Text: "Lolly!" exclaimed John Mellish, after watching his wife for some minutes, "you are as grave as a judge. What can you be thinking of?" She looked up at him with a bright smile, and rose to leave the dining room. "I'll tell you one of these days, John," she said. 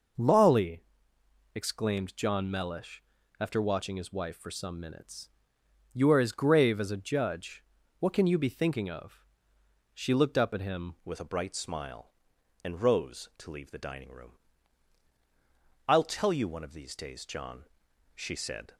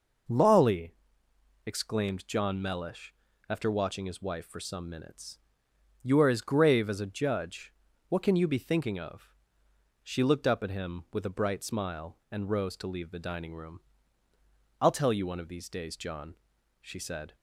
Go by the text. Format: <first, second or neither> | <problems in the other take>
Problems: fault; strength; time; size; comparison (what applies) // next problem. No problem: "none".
second | changes voice at "with"; from 11.0 s on; 7.7 s long